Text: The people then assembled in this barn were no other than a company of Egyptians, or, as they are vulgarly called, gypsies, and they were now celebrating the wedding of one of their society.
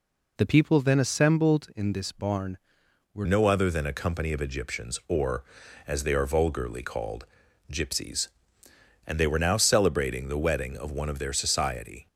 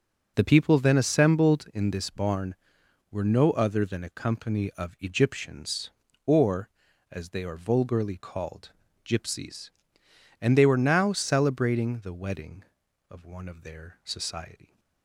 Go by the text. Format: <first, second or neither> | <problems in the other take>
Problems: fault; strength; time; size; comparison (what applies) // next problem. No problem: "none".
second | changes voice at "no"; from 3.2 s on; 8.8 s long